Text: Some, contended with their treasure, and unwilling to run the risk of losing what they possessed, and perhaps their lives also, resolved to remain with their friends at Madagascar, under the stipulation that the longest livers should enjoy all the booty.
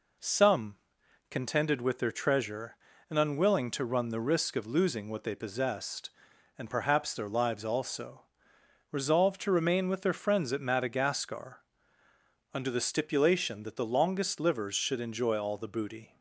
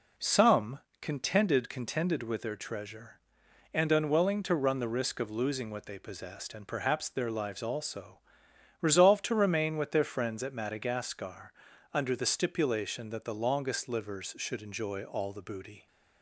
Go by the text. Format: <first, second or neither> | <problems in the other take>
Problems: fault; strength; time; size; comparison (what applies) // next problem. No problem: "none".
first | says "contended" twice; at 1.6 s